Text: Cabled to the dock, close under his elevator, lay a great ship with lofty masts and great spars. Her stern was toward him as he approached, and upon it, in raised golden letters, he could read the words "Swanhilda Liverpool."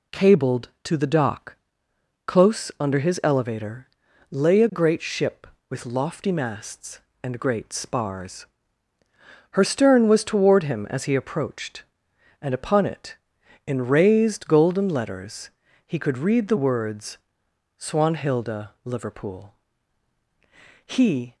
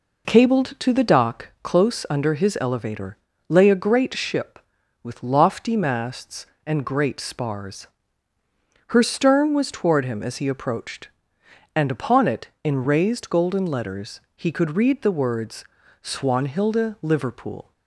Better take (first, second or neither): second